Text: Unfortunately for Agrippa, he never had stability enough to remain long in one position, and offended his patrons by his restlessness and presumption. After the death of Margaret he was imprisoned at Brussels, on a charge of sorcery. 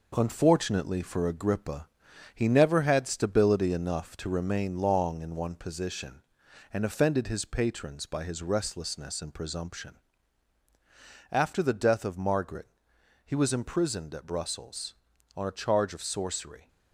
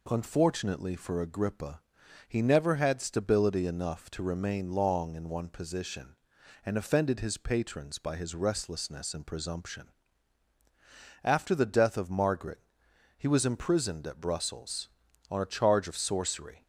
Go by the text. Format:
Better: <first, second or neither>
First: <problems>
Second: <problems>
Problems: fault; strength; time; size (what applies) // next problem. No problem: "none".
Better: second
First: gets quieter; noticeable; throughout; 5 dB // pauses between "Margaret" and "he"; noticeable; at 12.6 s; 0.58 s long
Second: pauses between "Margaret" and "he"; noticeable; at 12.5 s; 0.58 s long